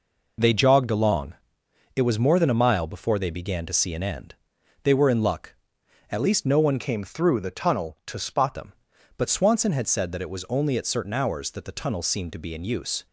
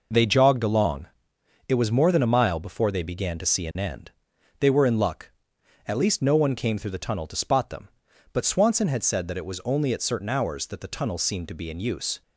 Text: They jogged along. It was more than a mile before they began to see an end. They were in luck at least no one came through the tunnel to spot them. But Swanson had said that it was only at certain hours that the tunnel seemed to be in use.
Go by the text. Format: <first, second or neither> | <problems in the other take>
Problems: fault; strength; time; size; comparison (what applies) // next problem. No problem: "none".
second | changes voice from "came" to "spot"; from 6.7 to 8.5 s; 1.8 s long